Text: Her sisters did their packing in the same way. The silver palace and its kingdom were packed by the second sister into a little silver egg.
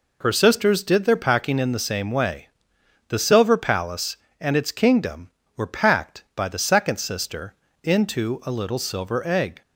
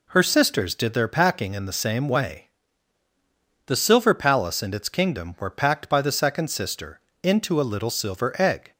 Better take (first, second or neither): neither